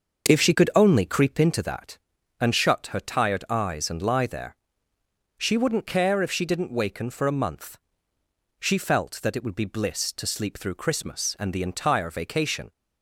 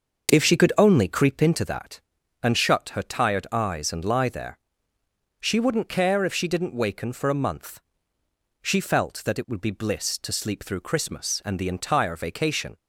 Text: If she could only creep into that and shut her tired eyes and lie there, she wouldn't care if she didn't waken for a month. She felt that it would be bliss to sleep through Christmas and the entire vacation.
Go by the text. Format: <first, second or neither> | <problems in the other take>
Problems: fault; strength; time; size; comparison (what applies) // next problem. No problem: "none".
neither | starts louder than the rest; the same in both